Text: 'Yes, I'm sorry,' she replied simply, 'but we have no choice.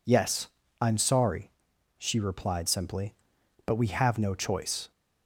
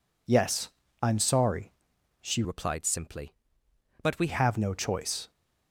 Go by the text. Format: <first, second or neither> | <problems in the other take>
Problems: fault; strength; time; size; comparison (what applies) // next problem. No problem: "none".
first | changes voice from "replied" to "we"; from 2.4 to 4.2 s; 1.8 s long